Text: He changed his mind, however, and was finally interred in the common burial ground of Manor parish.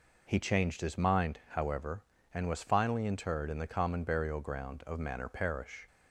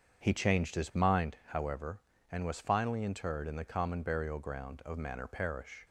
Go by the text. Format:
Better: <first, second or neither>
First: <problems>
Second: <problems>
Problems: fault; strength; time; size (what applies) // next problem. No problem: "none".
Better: first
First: none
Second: starts louder than the rest; strong; until 1.4 s; 7 dB